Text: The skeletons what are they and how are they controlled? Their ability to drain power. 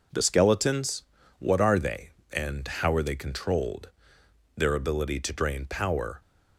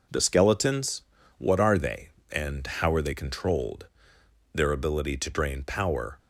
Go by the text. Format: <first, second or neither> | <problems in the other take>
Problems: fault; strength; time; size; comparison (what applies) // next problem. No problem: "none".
neither | pauses between "skeletons" and "what"; slight; the same in both